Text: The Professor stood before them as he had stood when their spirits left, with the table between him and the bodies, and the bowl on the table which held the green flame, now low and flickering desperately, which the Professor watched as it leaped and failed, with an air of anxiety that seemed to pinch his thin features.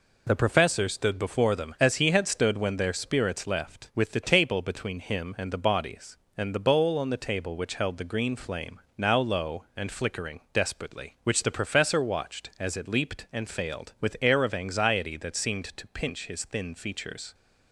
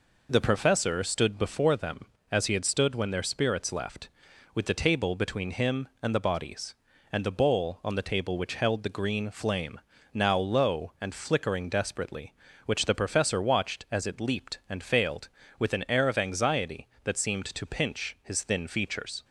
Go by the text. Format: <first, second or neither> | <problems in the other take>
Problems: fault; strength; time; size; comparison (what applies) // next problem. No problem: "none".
second | skips "an"; at 14.1 s